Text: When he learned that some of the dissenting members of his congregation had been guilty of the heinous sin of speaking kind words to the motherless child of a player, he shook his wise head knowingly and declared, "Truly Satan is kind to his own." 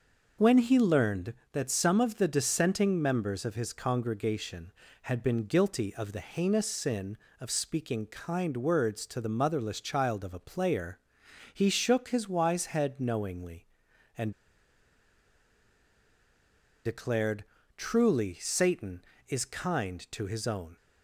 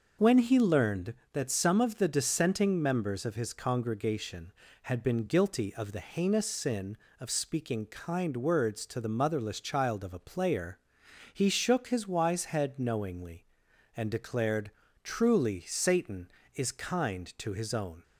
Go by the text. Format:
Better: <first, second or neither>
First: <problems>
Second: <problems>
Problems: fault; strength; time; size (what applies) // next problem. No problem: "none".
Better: second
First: starts louder than the rest; noticeable; until 1.5 s; 6 dB // pauses between "and" and "declared"; strong; at 14.3 s; 2.5 s long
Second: starts louder than the rest; noticeable; until 1.3 s; 6 dB